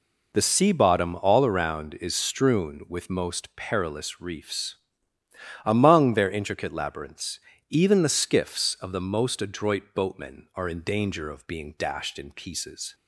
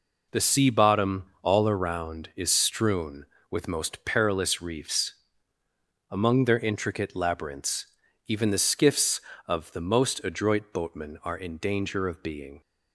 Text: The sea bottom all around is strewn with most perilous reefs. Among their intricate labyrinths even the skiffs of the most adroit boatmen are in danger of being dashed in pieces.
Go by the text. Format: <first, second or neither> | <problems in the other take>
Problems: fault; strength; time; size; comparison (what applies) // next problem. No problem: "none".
first | pauses between "bottom" and "all"; slight; at 1.2 s; 0.16 s long // pauses between "labyrinths" and "even"; at 7.8 s; 0.40 s long; slight in the first // stops before "dashed in pieces"; at 12.6 s